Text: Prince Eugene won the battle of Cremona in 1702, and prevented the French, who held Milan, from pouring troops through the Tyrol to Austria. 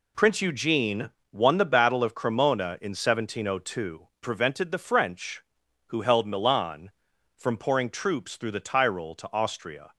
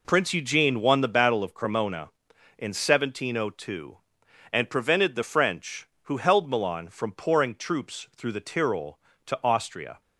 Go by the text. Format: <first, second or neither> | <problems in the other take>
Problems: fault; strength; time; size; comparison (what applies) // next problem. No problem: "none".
second | pauses between "Eugene" and "won"; slight; at 1.0 s; 0.20 s long // skips "and"; at 4.1 s